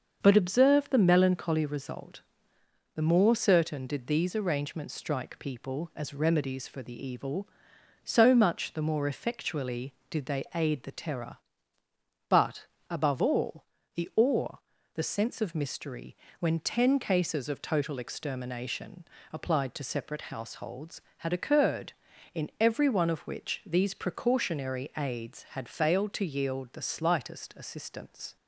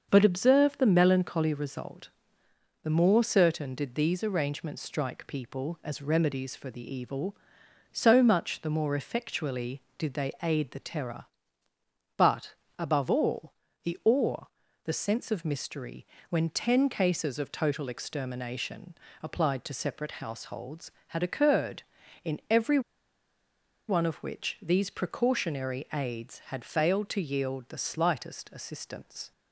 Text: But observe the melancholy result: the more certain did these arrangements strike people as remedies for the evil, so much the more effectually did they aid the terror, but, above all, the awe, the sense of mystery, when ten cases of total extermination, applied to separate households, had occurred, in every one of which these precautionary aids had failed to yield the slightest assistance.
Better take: first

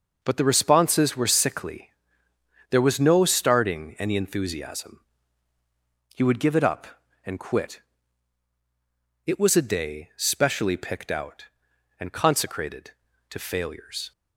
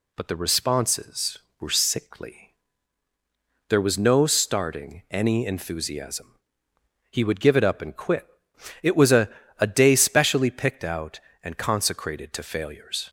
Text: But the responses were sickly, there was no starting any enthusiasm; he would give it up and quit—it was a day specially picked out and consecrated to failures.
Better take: first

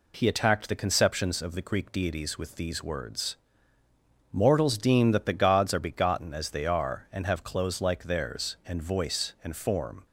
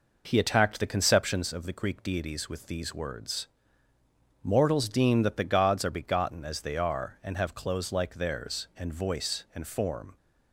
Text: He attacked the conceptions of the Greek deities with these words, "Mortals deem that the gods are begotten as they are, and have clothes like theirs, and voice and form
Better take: first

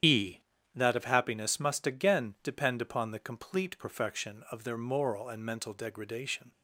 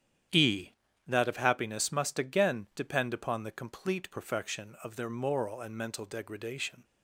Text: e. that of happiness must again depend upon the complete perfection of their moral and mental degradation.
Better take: second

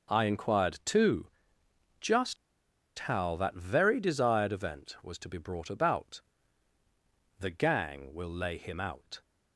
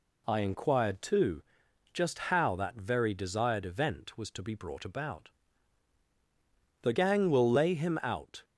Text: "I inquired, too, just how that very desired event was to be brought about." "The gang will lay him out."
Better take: second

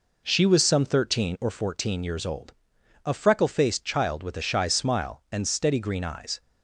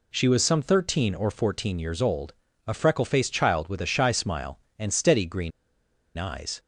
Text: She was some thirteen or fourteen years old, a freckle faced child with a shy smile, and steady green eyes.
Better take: first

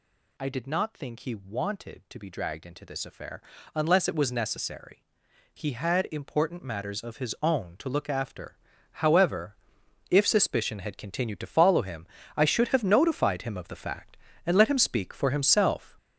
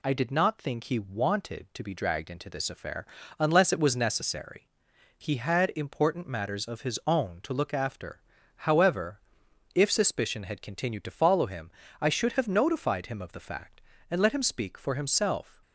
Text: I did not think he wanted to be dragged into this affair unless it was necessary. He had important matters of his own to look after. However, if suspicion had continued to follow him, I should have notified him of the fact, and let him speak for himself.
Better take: second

